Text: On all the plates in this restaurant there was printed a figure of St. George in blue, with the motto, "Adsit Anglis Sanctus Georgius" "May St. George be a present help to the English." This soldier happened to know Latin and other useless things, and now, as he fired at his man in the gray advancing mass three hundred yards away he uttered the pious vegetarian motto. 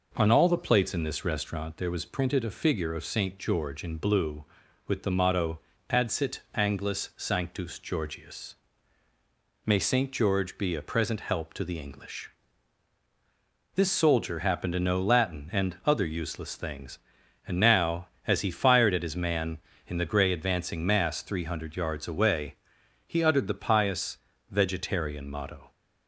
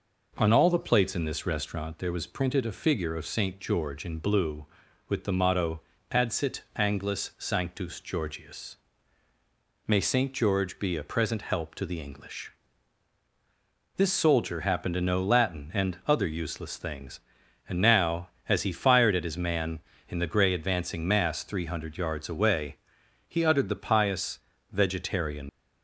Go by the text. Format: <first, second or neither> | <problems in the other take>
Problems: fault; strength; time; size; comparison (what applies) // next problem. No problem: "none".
first | pauses between "Georgius" and "May"; at 8.7 s; 1.0 s long; also in the first // pauses between "away" and "he"; noticeable; at 22.7 s; 0.50 s long; noticeable in the first // pauses between "pious" and "vegetarian"; slight; at 24.3 s; 0.32 s long; slight in the first // stops before "motto"; at 25.4 s